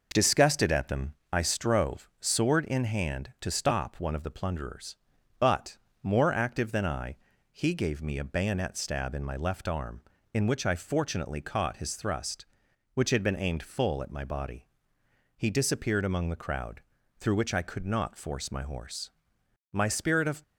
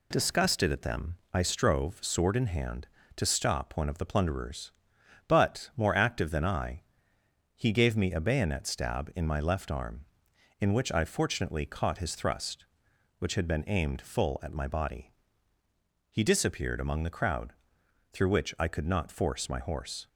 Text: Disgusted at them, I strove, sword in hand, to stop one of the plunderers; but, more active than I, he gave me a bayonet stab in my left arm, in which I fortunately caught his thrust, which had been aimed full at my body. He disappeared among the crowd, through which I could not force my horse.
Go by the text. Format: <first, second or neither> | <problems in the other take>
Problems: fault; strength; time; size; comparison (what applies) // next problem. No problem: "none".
second | goes on to say "My spirit of"; noticeable; from 19.7 s on; 0.70 s long